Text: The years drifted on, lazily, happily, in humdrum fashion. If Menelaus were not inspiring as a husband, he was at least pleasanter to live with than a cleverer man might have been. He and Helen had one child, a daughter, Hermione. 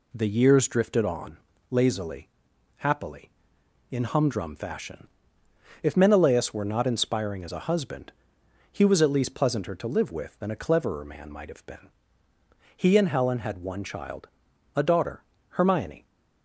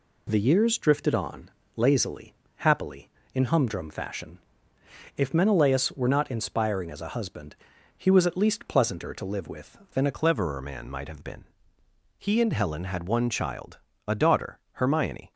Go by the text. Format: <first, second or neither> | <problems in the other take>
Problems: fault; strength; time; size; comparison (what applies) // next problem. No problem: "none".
first | changes voice at "cleverer"; from 10.1 s on; 5.2 s long